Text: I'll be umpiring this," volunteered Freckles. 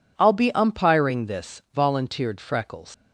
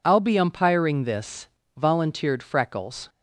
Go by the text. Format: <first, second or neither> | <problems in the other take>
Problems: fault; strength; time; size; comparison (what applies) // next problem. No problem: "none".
second | leaves "Freckles" unfinished; at 2.9 s; 110 ms